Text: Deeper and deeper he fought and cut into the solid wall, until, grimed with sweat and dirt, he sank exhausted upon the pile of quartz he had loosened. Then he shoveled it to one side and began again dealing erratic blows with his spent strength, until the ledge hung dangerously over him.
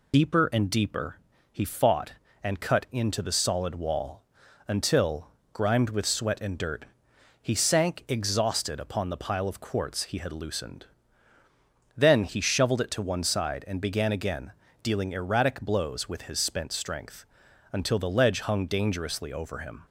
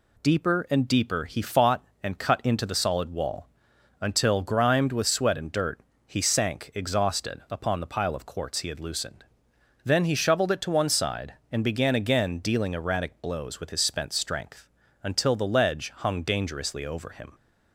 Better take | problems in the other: second | loses the start of "Deeper"; at 0.1 s; 45 ms // pauses between "deeper" and "he"; slight; at 1.1 s; 0.34 s long // pauses between "again" and "dealing"; slight; at 14.5 s; 0.30 s long

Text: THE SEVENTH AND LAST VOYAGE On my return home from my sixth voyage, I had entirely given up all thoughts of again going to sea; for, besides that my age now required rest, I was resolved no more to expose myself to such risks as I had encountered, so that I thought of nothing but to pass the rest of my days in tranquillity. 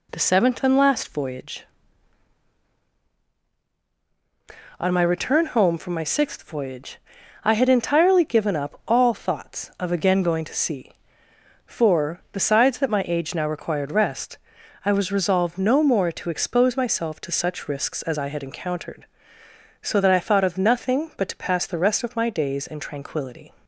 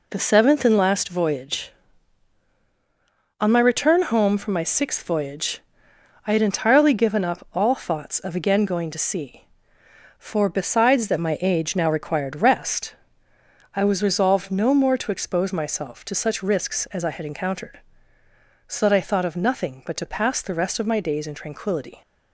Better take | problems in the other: neither | none

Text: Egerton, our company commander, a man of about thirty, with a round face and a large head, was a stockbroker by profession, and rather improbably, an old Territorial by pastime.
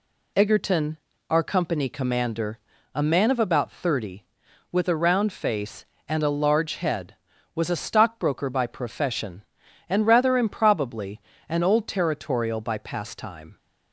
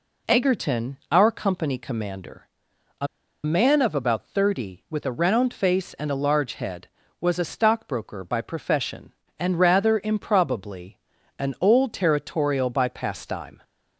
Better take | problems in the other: first | pauses between "a" and "man"; at 3.0 s; 0.37 s long

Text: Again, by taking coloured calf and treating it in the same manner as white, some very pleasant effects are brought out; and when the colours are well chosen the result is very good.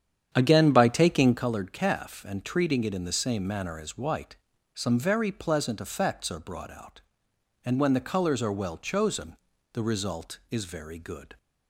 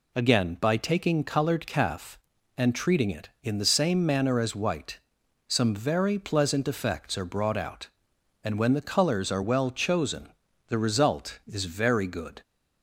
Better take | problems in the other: second | starts louder than the rest; strong; until 1.5 s; 9 dB // pauses between "chosen" and "the"; slight; at 9.3 s; 0.34 s long; also in the second

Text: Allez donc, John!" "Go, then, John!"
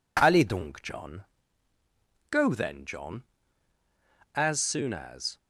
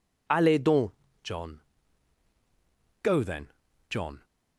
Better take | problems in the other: second | goes on to say "As soon as"; noticeable; from 4.3 s on; 1.0 s long

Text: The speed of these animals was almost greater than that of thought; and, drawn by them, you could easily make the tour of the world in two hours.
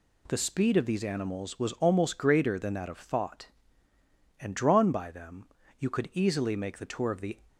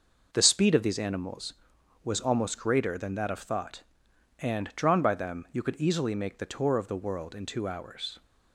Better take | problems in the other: second | stops before "world in two hours"; at 7.4 s

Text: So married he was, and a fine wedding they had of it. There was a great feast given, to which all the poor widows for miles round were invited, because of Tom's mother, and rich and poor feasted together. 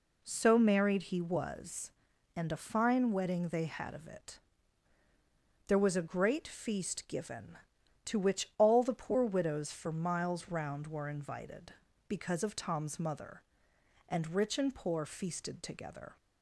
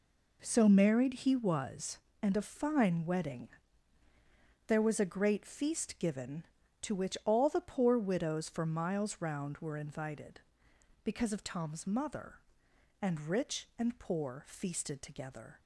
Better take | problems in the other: first | skips "they had of it"; at 4.0 s

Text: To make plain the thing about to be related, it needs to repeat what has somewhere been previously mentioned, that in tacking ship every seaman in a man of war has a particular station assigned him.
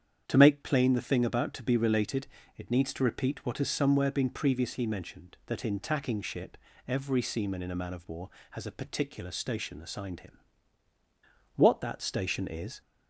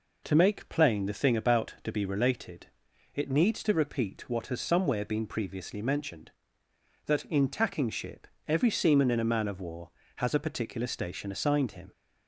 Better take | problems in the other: second | starts louder than the rest; strong; until 1.3 s; 8.5 dB // pauses between "ship" and "every"; slight; at 6.5 s; 0.32 s long; slight in the second // goes on to say "What that station is"; noticeable; from 11.5 s on; 1.2 s long

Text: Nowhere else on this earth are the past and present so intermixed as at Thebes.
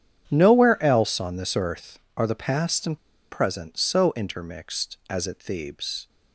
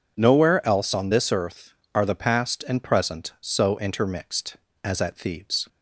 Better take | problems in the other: second | starts louder than the rest; strong; until 1.3 s; 9 dB // pauses between "and" and "present"; slight; at 2.9 s; 0.34 s long

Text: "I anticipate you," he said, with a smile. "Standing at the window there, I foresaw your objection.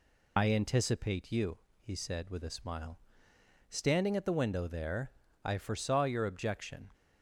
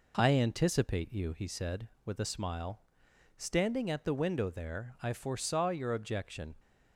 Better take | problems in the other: second | loses the start of "I"; at 0.3 s; 45 ms

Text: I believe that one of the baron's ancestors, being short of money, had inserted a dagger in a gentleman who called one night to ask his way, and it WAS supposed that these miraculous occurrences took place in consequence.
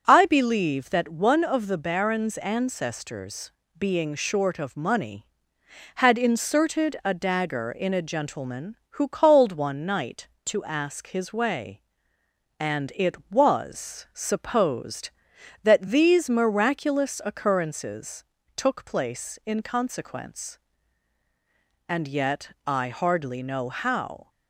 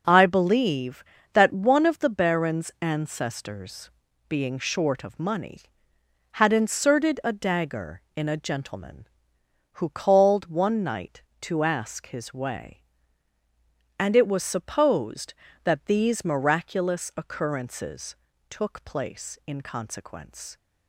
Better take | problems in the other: second | starts louder than the rest; until 1.0 s; 6.5 dB // pauses between "occurrences" and "took"; slight; at 18.2 s; 0.32 s long; slight in the second // goes on to say "And yet I hardly know how"; strong; from 21.8 s on; 2.4 s long

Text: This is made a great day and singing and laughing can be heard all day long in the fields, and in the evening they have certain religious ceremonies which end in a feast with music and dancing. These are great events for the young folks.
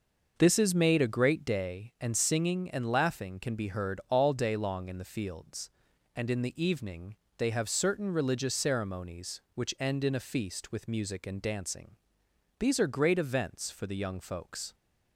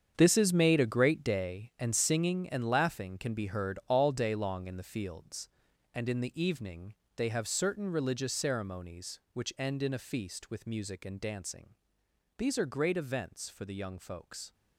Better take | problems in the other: first | gets quieter; strong; throughout; 12 dB // starts louder than the rest; strong; until 1.1 s; 7.5 dB; noticeable in the first // pauses between "evening" and "they"; slight; at 6.9 s; 0.22 s long; slight in the first

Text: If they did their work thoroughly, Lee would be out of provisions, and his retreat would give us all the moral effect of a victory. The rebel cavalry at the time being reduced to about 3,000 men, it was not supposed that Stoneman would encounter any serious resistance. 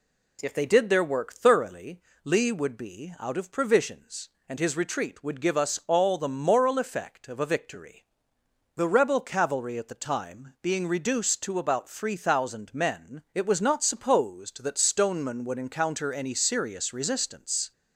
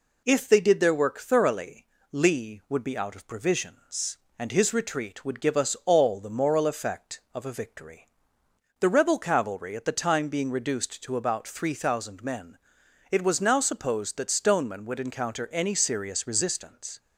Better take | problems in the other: first | says "now" for "not"; at 13.4 s

